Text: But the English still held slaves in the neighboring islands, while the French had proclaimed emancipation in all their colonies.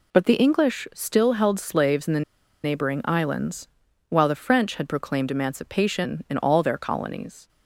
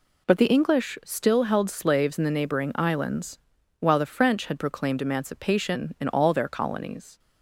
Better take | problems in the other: second | pauses between "the" and "neighboring"; at 2.2 s; 0.42 s long

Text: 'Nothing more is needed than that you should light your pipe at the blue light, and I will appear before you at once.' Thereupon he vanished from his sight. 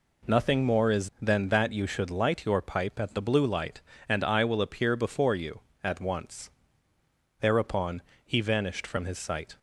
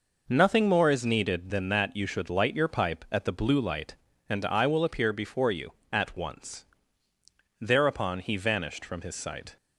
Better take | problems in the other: second | skips "needed"; at 1.1 s // pauses between "Thereupon" and "he"; slight; at 8.0 s; 0.22 s long

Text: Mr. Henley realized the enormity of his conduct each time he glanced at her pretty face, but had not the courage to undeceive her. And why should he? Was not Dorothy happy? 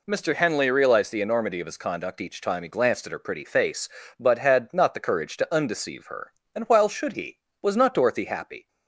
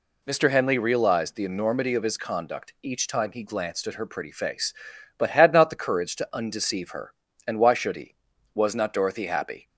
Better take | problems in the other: second | says "while" for "why"; at 6.6 s

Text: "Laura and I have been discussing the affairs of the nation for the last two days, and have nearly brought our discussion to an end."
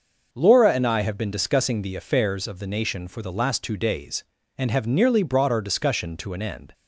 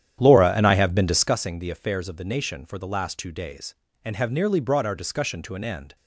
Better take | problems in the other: first | starts louder than the rest; strong; until 1.4 s; 10 dB

